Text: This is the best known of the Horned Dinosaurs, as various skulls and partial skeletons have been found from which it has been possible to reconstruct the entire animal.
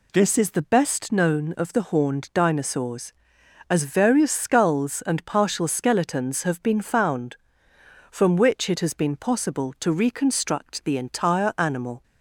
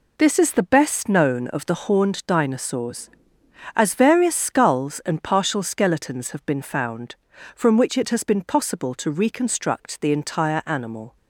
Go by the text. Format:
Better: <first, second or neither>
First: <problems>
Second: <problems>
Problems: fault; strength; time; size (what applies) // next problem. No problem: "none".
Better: neither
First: none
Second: none